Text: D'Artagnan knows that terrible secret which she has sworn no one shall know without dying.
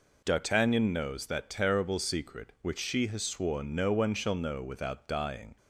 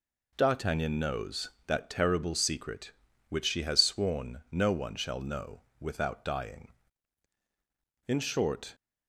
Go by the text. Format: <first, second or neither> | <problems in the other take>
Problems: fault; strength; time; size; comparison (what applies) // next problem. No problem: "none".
first | pauses between "know" and "without"; slight; at 5.6 s; 0.34 s long // goes on to say "In short"; noticeable; from 8.0 s on; 0.66 s long